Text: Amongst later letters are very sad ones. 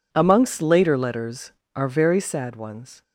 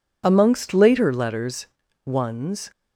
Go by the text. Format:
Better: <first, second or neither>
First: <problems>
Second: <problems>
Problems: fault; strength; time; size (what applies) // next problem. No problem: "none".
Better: first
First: none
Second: skips "are very sad"; at 1.8 s